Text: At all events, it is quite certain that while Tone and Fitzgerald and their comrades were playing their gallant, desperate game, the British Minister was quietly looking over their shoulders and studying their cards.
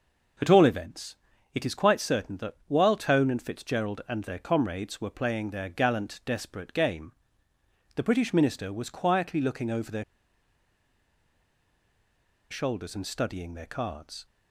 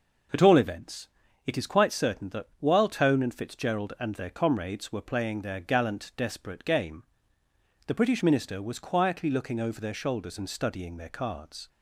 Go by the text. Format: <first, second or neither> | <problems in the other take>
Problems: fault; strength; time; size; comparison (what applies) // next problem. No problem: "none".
second | pauses between "their" and "shoulders"; strong; at 10.0 s; 2.4 s long